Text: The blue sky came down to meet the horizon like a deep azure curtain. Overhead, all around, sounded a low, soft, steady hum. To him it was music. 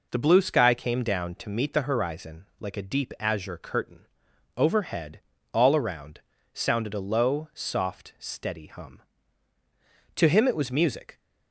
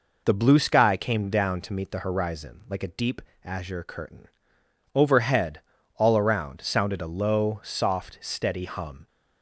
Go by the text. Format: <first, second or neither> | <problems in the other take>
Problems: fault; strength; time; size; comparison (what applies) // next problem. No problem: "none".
first | pauses between "deep" and "azure"; slight; at 3.2 s; 0.22 s long // stops before "To him it was music"; at 9.0 s